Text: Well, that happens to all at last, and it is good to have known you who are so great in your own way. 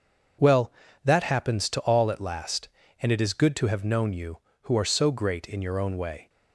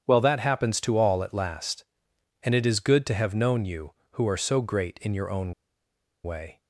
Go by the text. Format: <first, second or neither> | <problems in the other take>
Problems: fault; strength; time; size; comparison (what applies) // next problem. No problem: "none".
first | starts louder than the rest; strong; until 1.0 s; 8.5 dB // pauses between "own" and "way"; noticeable; at 5.5 s; 0.71 s long